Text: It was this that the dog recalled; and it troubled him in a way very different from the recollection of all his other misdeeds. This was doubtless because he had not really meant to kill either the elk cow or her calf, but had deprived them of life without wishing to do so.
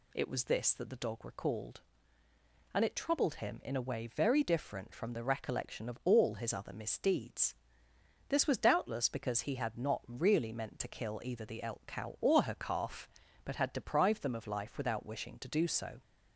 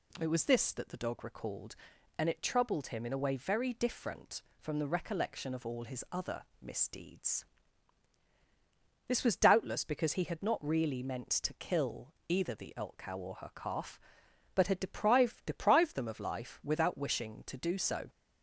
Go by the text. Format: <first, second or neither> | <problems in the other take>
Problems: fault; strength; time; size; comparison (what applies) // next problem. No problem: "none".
first | pauses between "other" and "misdeeds"; slight; at 6.4 s; 0.18 s long // says "deprived" twice; at 15.4 s